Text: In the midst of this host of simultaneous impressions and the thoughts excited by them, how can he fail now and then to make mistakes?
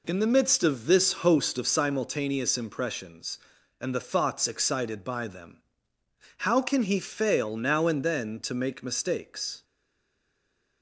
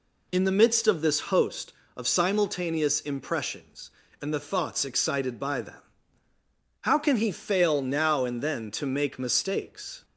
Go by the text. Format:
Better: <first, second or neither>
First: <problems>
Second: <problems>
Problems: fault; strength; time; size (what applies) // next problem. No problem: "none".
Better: second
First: stays silent after the last word; noticeable; from 9.6 s on; 1.2 s long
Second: none